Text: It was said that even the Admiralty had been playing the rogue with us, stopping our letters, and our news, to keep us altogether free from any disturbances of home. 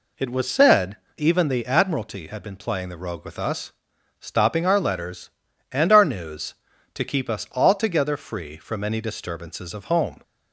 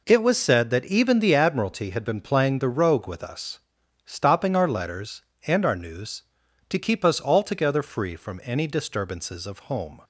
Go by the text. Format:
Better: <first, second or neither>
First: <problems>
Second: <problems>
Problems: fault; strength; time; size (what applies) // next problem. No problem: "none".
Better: second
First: skips "that"; at 1.0 s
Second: none